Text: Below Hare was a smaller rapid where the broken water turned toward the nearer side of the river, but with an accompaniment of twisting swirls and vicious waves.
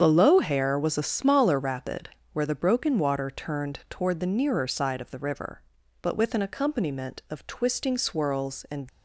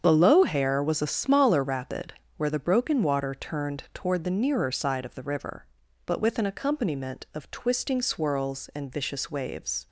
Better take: second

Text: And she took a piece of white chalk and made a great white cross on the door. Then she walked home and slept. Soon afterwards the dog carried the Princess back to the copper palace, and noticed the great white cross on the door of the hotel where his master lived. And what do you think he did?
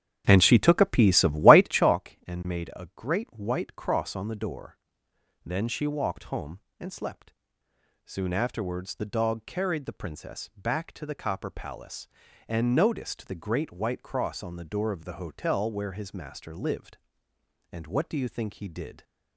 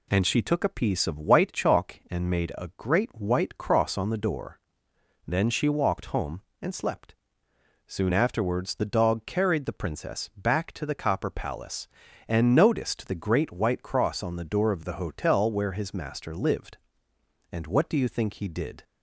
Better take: second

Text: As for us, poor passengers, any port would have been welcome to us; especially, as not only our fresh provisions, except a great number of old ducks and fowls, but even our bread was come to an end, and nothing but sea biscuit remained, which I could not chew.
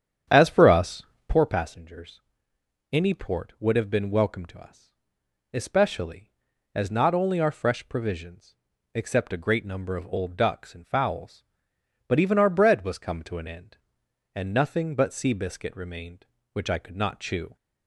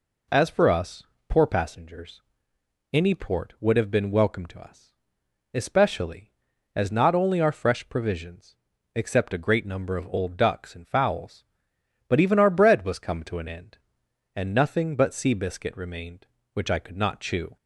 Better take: second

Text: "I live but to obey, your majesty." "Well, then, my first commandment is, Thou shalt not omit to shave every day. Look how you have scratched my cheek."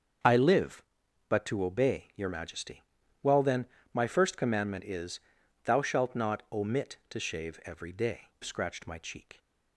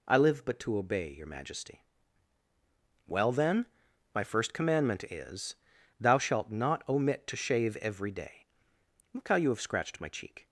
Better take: second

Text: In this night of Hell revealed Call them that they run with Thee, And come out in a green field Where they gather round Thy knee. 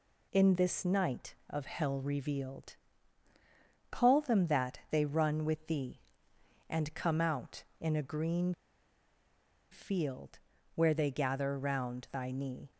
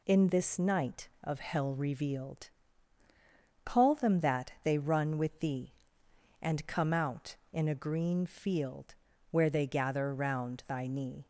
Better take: second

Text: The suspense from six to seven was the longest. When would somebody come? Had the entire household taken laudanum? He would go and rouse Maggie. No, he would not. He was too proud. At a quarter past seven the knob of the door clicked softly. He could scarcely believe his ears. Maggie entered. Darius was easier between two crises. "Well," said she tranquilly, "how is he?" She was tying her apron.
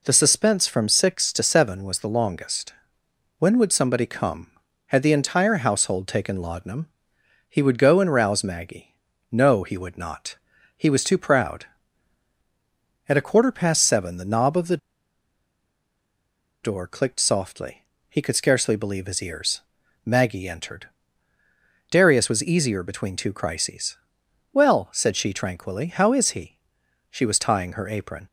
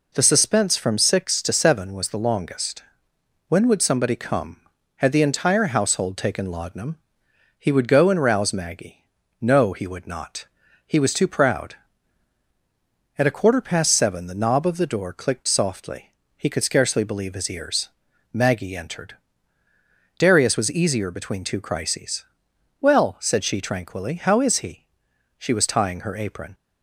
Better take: second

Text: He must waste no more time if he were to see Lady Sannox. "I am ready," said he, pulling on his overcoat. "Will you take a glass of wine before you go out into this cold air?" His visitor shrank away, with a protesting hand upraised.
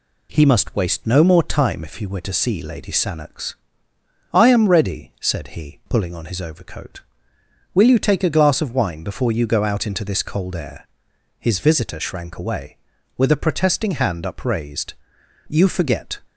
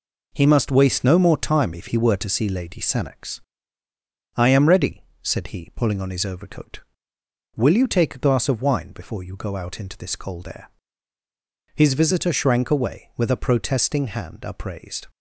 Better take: second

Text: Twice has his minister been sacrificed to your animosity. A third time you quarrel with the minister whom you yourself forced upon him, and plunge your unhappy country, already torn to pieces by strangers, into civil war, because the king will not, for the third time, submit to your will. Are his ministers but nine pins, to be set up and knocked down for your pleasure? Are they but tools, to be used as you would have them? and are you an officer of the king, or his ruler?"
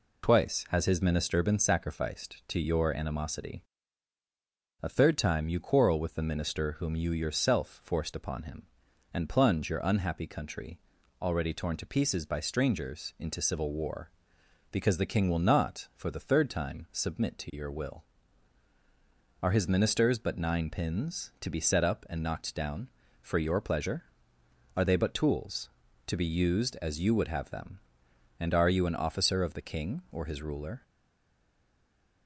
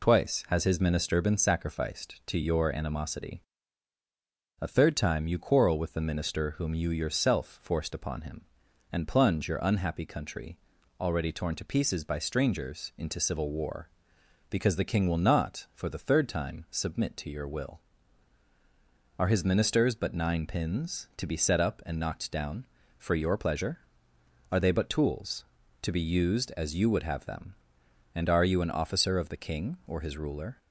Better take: second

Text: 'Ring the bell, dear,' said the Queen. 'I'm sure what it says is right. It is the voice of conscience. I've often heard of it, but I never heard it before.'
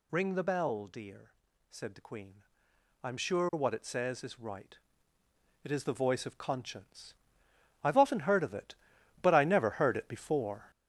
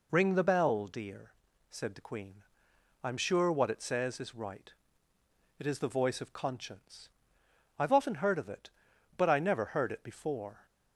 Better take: second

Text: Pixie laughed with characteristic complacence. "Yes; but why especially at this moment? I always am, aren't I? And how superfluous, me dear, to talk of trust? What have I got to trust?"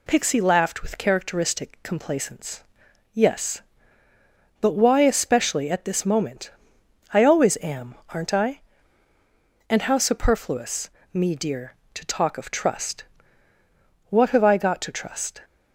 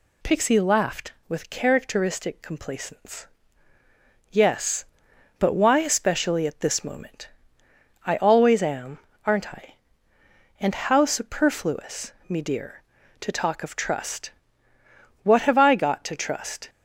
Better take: neither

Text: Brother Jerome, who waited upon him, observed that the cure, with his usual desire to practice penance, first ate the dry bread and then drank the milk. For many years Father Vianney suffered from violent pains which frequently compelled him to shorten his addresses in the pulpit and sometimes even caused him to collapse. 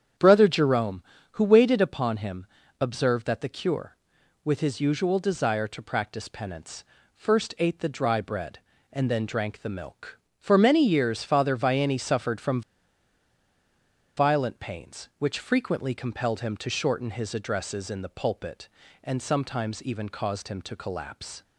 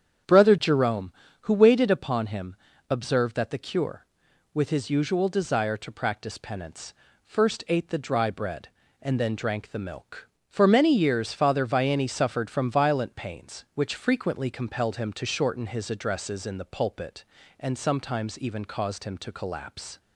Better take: second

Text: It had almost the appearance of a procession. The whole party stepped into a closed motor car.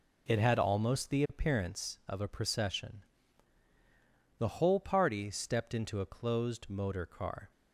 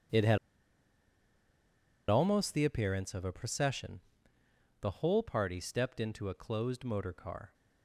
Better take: first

